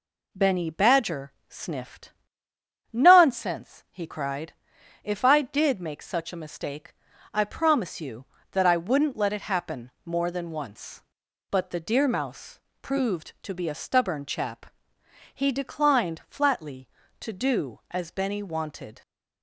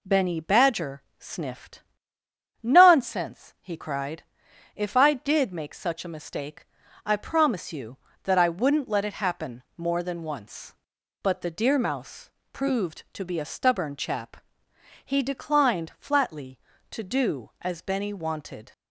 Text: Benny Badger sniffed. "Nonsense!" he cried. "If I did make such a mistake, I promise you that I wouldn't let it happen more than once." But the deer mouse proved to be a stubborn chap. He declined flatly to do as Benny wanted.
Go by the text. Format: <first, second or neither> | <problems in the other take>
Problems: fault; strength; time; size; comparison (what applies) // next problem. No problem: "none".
neither | pauses between "Badger" and "sniffed"; slight; the same in both // pauses between "happen" and "more"; slight; the same in both // pauses between "mouse" and "proved"; slight; the same in both